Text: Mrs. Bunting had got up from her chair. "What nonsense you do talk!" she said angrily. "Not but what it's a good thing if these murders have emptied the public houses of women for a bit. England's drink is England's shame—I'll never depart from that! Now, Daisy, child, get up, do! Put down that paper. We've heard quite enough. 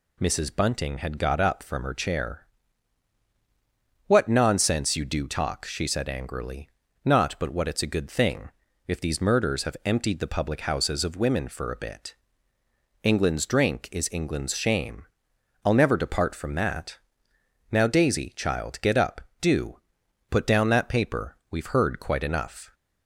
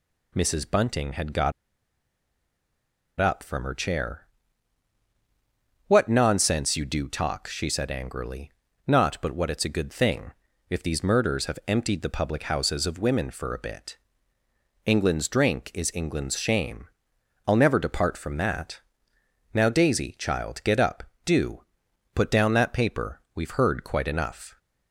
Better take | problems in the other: first | pauses between "got" and "up"; strong; at 1.5 s; 1.6 s long // pauses between "thing" and "if"; at 10.3 s; 0.38 s long; also in the first

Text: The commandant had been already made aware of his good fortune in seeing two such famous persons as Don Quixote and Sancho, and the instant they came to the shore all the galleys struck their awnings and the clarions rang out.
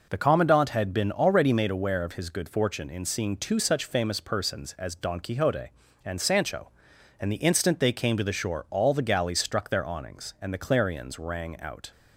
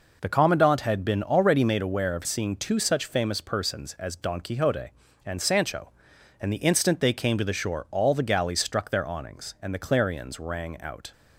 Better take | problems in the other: first | skips "his good fortune in"; at 2.2 s

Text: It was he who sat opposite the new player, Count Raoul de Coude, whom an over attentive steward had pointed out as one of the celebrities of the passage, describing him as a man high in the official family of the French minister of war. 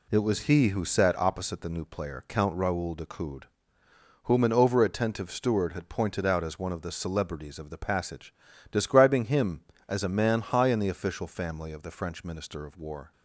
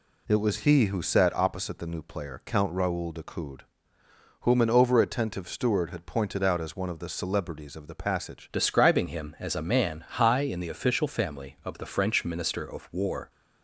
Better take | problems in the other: first | changes voice at "describing"; from 8.5 s on; 4.7 s long

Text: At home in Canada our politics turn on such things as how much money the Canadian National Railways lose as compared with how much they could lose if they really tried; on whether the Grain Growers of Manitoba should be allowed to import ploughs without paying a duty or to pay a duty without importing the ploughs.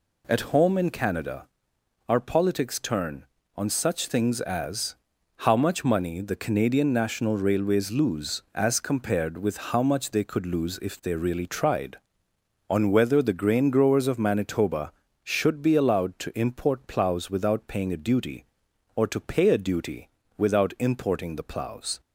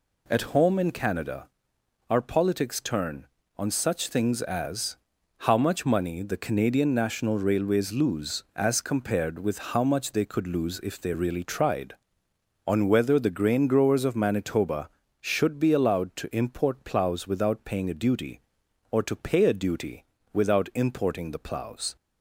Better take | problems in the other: neither | pauses between "Canada" and "our"; noticeable; the same in both // pauses between "as" and "how"; the same in both // pauses between "duty" and "without"; slight; the same in both

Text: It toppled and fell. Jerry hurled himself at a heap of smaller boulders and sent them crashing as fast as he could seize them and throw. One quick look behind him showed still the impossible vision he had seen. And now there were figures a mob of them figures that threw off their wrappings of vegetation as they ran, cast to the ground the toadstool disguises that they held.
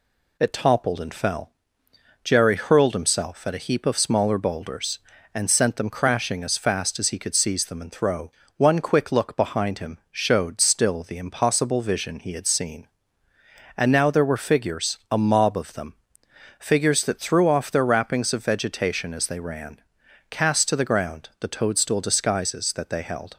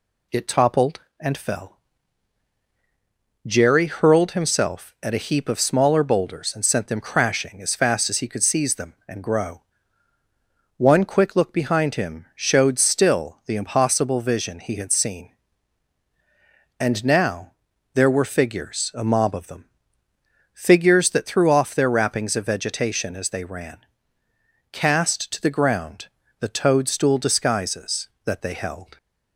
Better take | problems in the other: first | says "grow" for "throw"; at 9.2 s // pauses between "now" and "there"; at 17.5 s; 0.40 s long // pauses between "them" and "figures"; noticeable; at 19.6 s; 0.88 s long; noticeable in the first // pauses between "ground" and "the"; slight; at 26.0 s; 0.32 s long

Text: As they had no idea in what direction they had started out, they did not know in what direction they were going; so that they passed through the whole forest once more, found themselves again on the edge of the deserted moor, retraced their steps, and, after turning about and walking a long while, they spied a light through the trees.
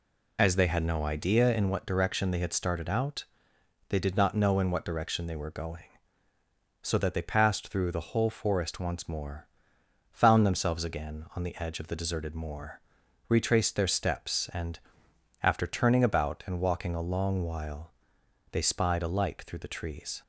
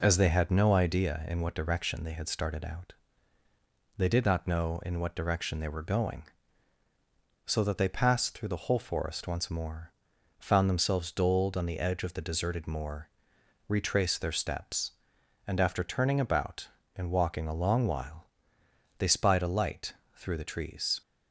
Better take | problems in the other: first | says "doled" for "again"; at 11.1 s // pauses between "light" and "through"; slight; at 19.9 s; 0.22 s long

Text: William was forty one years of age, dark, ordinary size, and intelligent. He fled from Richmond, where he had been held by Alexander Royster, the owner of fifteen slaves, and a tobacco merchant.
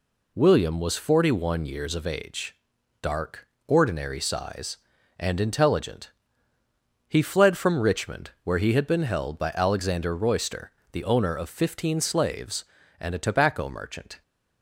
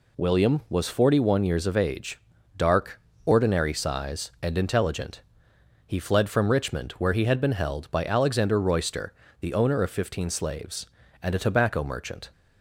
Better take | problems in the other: neither | none

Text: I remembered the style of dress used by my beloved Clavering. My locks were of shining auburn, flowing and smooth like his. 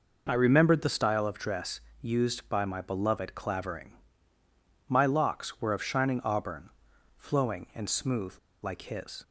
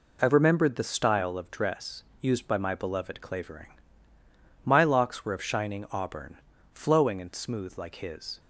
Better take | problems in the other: second | pauses between "dress" and "used"; slight; at 1.7 s; 0.22 s long; slight in the second // pauses between "smooth" and "like"; slight; at 8.3 s; 0.26 s long

